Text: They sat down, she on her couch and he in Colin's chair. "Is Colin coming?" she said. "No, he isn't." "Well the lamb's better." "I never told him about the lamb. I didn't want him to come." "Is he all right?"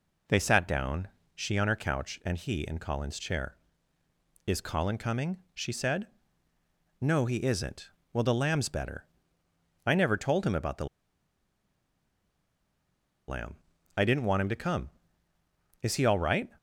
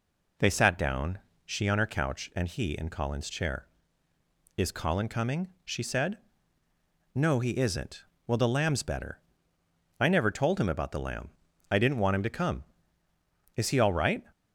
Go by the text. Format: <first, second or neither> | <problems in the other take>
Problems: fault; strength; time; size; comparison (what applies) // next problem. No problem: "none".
second | pauses between "the" and "lamb"; strong; at 10.8 s; 2.4 s long